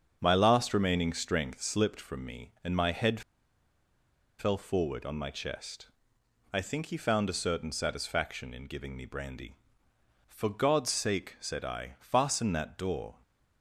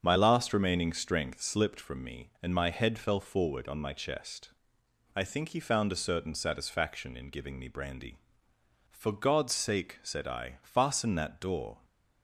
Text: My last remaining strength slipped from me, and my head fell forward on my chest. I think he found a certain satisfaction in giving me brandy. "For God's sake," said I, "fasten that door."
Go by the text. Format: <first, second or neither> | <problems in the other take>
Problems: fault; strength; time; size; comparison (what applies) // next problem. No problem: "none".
second | starts louder than the rest; strong; until 1.2 s; 7.5 dB; strong in the second // pauses between "head" and "fell"; at 3.2 s; 1.1 s long